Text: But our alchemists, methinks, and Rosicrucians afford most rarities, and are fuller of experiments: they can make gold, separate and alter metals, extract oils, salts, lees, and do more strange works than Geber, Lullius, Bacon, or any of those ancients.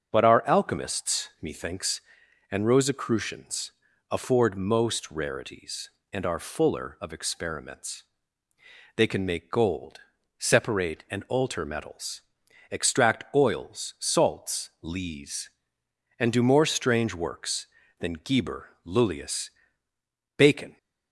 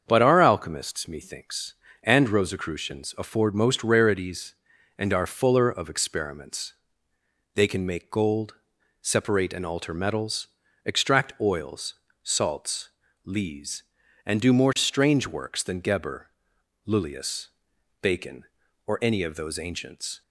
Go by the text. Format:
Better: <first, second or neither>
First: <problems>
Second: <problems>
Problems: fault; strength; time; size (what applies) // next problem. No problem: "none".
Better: second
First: starts louder than the rest; until 1.1 s; 6.5 dB // pauses between "Rosicrucians" and "afford"; at 3.7 s; 0.38 s long // stops before "or any of those ancients"; at 20.7 s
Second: starts louder than the rest; until 1.0 s; 7 dB